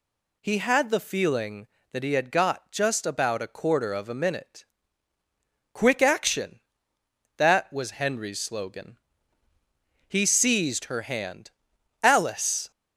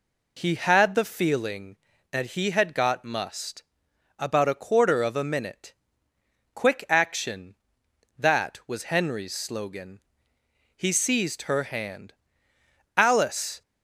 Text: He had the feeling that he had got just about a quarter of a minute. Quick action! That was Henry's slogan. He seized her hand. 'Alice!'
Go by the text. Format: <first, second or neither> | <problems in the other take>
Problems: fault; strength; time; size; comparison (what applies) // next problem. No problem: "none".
first | says "must" for "just"; at 3.0 s